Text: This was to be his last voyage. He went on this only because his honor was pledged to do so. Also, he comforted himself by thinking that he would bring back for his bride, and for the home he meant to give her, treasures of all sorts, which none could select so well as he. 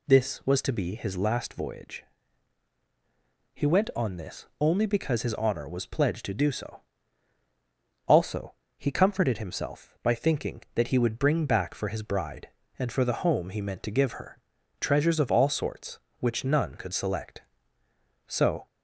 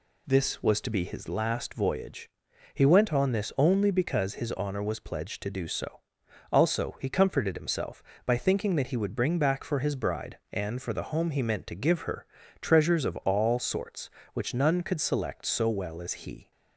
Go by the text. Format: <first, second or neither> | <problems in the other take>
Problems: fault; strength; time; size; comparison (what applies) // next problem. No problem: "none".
second | stops before "well as he"; at 18.6 s